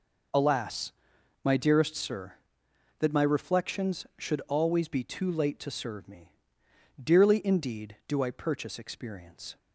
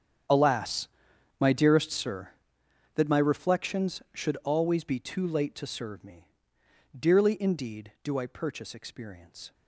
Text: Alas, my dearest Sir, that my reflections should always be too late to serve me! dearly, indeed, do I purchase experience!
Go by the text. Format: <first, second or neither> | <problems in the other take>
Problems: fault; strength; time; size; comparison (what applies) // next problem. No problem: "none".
first | gets quieter; strong; throughout; 18 dB